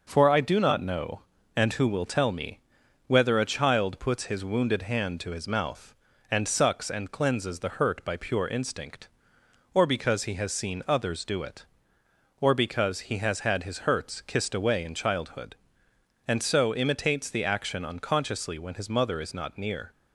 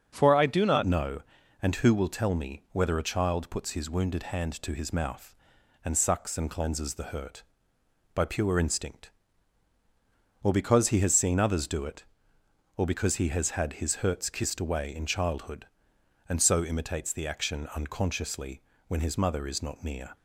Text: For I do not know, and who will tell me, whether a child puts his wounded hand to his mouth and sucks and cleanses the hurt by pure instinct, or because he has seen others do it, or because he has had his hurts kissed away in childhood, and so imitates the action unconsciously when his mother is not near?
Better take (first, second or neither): first